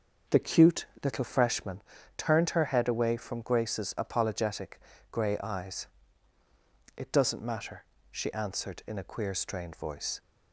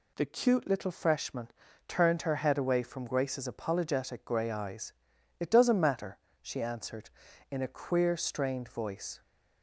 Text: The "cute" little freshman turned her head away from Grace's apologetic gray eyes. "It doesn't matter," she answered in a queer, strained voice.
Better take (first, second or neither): second